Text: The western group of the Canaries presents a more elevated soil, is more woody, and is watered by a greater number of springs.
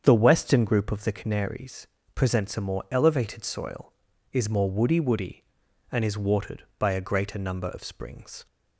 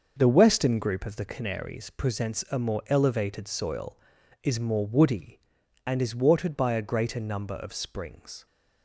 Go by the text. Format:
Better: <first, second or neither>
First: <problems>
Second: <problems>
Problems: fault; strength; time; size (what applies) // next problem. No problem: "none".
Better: second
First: starts louder than the rest; strong; until 1.0 s; 7.5 dB // pauses between "Canaries" and "presents"; slight; at 1.8 s; 0.28 s long // says "woody" twice; at 4.9 s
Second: starts louder than the rest; noticeable; until 1.1 s; 6 dB